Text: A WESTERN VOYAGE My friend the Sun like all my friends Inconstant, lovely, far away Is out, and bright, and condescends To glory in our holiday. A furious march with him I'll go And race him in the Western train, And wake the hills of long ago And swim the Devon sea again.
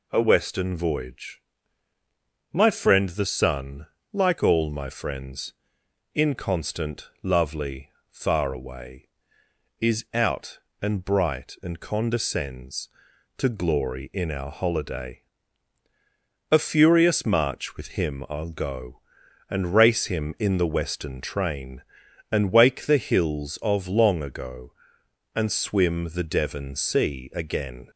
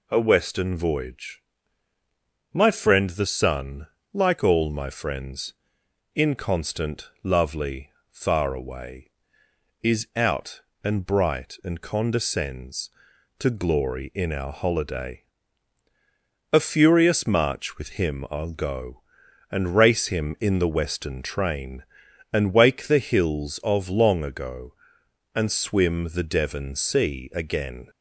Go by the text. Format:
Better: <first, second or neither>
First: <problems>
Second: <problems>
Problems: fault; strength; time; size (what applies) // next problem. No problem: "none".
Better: neither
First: pauses between "VOYAGE" and "My"; at 1.4 s; 1.1 s long // pauses between "Sun" and "like"; slight; at 3.8 s; 0.24 s long // pauses between "friends" and "Inconstant"; noticeable; at 5.5 s; 0.60 s long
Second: pauses between "VOYAGE" and "My"; at 1.4 s; 1.1 s long // pauses between "Sun" and "like"; slight; at 3.8 s; 0.24 s long // pauses between "friends" and "Inconstant"; noticeable; at 5.5 s; 0.60 s long